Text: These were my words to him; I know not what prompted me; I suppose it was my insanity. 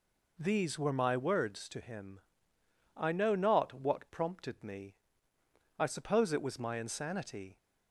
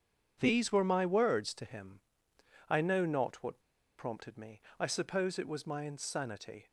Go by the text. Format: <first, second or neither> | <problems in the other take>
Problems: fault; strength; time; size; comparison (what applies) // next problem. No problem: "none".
first | pauses between "what" and "prompted"; at 3.5 s; 0.40 s long